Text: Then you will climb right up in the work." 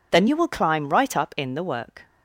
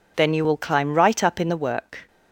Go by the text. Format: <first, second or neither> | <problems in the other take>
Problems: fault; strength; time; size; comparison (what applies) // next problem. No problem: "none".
neither | none